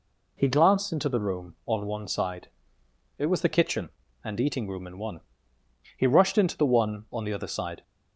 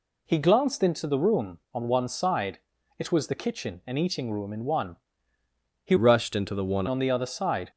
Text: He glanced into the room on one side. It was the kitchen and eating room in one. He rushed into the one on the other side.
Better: first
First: none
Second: changes voice from "rushed" to "one"; from 5.9 to 6.8 s; 0.9 s long

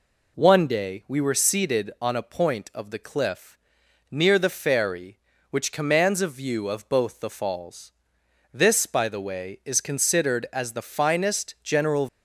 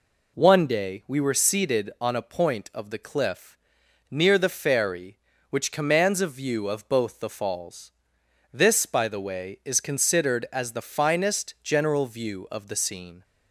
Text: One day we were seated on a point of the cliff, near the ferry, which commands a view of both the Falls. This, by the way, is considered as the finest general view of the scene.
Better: second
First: stops before "view of the scene"; at 12.0 s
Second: none

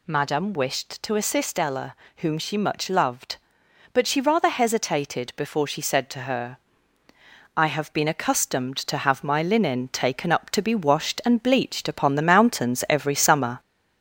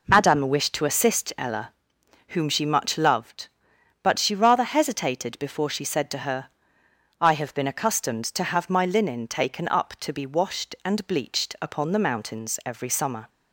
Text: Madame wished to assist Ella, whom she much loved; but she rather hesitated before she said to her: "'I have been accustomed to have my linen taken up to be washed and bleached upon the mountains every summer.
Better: second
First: gets louder; slight; throughout; 3.5 dB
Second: none

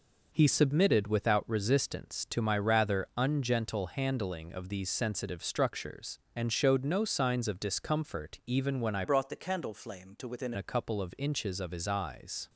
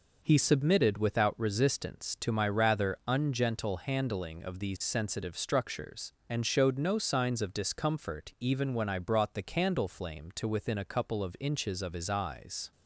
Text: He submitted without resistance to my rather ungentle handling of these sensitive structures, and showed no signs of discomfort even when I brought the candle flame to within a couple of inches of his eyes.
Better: second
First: changes voice from "brought" to "within"; from 9.0 to 10.5 s; 1.5 s long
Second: none

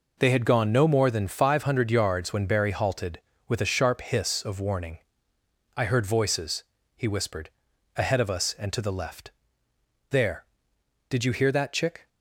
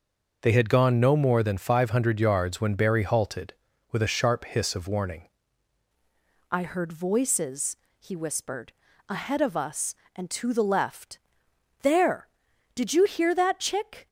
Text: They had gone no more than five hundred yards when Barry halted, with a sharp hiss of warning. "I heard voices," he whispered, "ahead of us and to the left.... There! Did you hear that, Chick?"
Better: first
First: none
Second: changes voice at "I"; from 6.5 s on; 7.5 s long

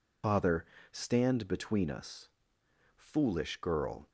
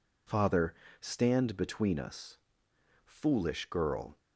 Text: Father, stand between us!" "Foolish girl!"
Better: second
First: loses the start of "Father"; at 0.2 s; 60 ms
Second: none

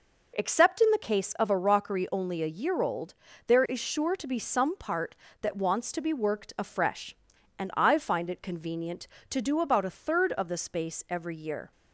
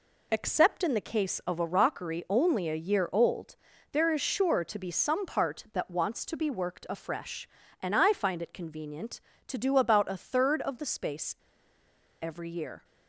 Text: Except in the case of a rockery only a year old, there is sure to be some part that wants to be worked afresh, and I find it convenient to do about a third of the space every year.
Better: first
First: none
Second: pauses between "space" and "every"; noticeable; at 11.3 s; 0.87 s long

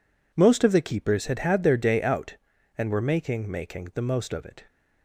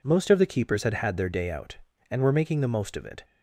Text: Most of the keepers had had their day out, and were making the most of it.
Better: second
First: says "making" twice; at 3.5 s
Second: none

